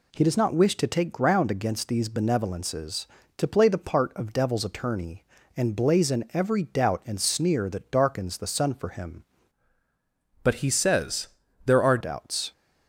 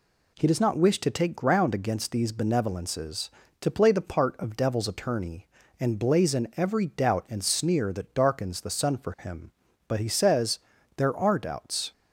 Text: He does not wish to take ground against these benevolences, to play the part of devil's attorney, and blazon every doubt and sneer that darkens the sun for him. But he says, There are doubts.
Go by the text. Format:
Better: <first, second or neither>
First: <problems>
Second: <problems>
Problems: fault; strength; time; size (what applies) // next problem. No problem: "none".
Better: second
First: changes voice from "But" to "are"; from 10.4 to 11.9 s; 1.5 s long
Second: none